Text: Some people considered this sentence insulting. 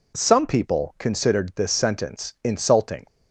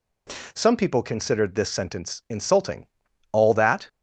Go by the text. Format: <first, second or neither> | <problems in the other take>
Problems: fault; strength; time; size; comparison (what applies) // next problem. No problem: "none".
first | goes on to say "All that"; from 3.3 s on; 0.56 s long